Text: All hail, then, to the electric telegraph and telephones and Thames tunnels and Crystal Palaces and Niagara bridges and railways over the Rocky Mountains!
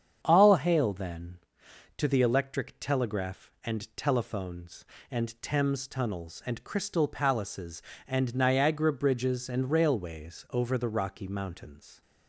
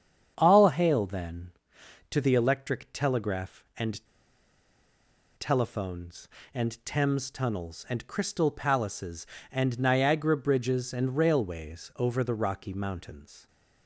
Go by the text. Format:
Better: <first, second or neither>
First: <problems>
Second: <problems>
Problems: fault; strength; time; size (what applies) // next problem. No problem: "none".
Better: first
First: starts louder than the rest; strong; until 1.2 s; 8 dB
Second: starts louder than the rest; strong; until 1.3 s; 8 dB // pauses between "and" and "telephones"; strong; at 4.0 s; 1.3 s long